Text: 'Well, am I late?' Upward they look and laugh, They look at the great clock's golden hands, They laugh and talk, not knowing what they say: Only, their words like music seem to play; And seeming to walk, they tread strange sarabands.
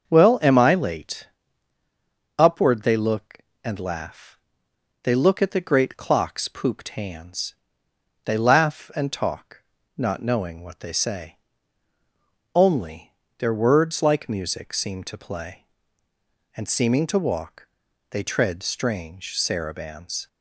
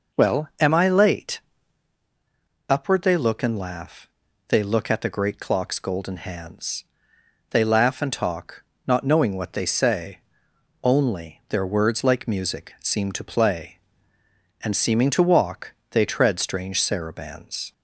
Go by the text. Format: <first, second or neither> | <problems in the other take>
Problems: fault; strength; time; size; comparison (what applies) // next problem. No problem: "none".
second | starts louder than the rest; until 1.1 s; 6.5 dB // says "pooped" for "golden"; at 6.4 s